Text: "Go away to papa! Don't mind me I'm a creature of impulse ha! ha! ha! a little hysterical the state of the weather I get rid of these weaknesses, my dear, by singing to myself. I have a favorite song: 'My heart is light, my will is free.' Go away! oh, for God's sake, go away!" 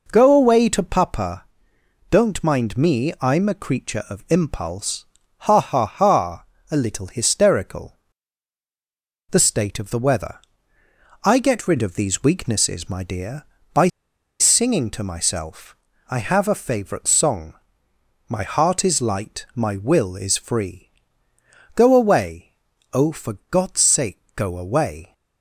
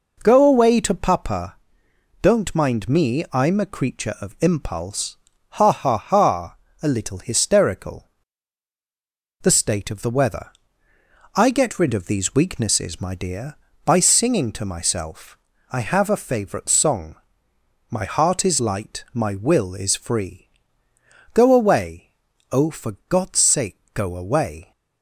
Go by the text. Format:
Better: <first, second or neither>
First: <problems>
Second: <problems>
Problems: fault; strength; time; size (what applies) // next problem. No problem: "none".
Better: second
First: pauses between "impulse" and "ha"; slight; at 5.0 s; 0.34 s long // pauses between "hysterical" and "the"; strong; at 7.9 s; 1.3 s long // pauses between "weather" and "I"; noticeable; at 10.3 s; 0.86 s long // pauses between "by" and "singing"; noticeable; at 13.8 s; 0.50 s long // pauses between "for" and "God's"; slight; at 23.3 s; 0.16 s long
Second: pauses between "impulse" and "ha"; slight; at 5.1 s; 0.34 s long // pauses between "hysterical" and "the"; strong; at 8.0 s; 1.3 s long // pauses between "weather" and "I"; noticeable; at 10.5 s; 0.86 s long // pauses between "for" and "God's"; slight; at 22.9 s; 0.16 s long